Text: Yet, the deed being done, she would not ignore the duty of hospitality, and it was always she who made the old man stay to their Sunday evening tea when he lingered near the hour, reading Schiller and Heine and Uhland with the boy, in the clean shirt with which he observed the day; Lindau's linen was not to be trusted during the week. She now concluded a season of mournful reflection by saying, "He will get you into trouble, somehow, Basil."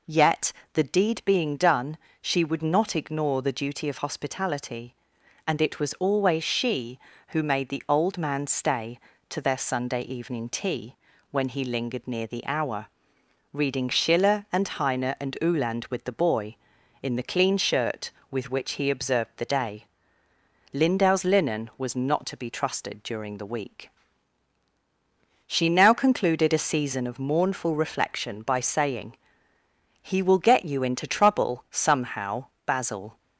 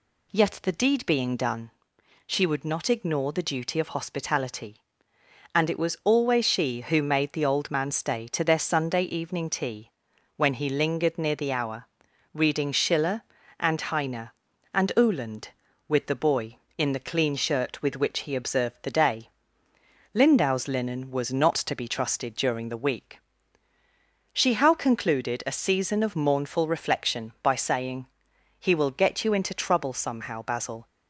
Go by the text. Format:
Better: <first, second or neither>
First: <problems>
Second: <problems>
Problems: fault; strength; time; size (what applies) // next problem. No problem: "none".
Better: first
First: pauses between "tea" and "when"; slight; at 10.9 s; 0.36 s long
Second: pauses between "tea" and "when"; noticeable; at 9.8 s; 0.48 s long // says "how" for "now"; at 24.5 s